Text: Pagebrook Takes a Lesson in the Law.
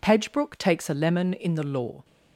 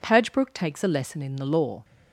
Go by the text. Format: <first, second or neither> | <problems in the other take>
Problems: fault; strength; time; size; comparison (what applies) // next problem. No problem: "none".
second | says "Lemon" for "Lesson"; at 0.9 s